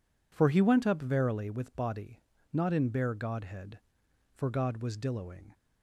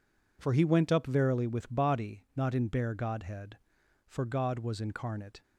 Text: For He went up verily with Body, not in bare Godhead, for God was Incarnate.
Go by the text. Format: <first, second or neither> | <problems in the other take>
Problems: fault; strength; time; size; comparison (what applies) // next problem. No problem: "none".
second | says "Dilloing" for "Incarnate"; at 4.9 s